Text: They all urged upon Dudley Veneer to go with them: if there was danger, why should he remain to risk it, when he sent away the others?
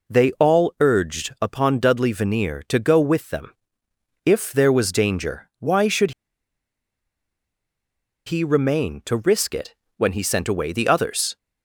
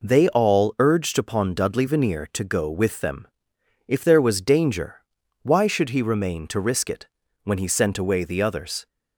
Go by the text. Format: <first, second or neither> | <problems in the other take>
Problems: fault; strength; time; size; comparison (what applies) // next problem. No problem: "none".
second | pauses between "should" and "he"; strong; at 6.1 s; 2.1 s long